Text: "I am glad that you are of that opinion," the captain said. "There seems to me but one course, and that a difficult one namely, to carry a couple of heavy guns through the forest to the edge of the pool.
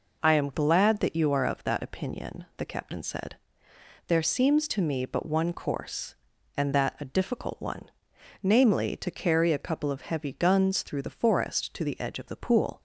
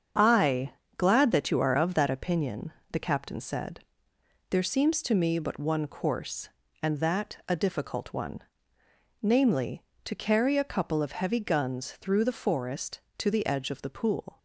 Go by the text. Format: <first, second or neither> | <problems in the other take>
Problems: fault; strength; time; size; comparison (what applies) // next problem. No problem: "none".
first | starts louder than the rest; strong; until 1.4 s; 7.5 dB // skips "am"; at 0.8 s // pauses between "one" and "namely"; noticeable; at 8.4 s; 0.80 s long; noticeable in the first